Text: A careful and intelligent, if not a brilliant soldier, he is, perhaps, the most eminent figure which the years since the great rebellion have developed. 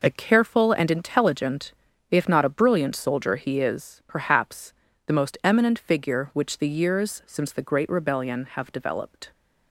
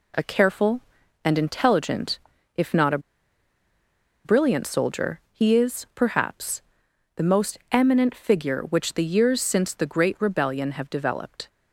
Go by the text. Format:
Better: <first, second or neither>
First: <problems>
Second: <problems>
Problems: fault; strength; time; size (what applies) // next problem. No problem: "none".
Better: first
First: none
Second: pauses between "a" and "brilliant"; strong; at 2.9 s; 1.2 s long